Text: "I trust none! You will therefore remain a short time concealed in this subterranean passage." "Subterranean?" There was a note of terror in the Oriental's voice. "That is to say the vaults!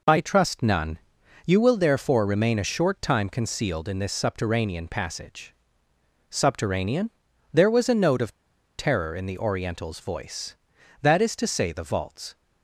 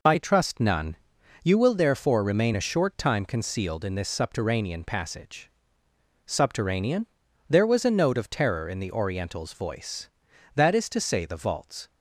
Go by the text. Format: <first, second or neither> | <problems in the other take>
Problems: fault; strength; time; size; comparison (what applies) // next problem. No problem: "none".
second | pauses between "of" and "terror"; at 8.3 s; 0.45 s long